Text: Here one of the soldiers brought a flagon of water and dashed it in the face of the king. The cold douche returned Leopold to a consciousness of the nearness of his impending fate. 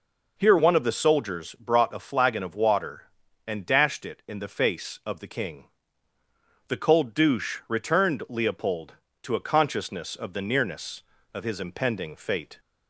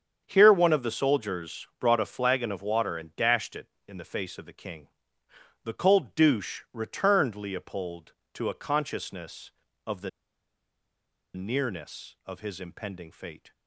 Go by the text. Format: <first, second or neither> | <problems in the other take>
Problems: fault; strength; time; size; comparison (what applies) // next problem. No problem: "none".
first | starts louder than the rest; strong; until 1.2 s; 7.5 dB // pauses between "the" and "nearness"; strong; at 10.0 s; 1.2 s long